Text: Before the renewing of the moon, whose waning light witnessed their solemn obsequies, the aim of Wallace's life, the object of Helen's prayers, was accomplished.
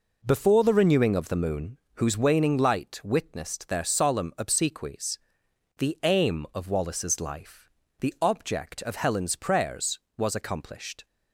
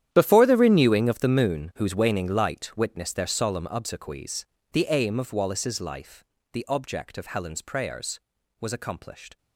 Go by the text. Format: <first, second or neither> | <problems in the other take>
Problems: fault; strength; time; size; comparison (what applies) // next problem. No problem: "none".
first | gets quieter; strong; throughout; 16.5 dB